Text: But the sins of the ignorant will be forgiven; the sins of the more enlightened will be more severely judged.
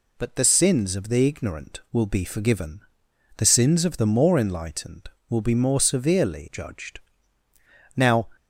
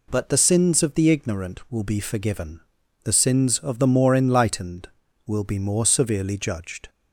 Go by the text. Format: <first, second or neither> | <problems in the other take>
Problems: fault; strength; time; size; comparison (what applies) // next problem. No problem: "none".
second | goes on to say "Now"; slight; from 7.9 s on; 0.32 s long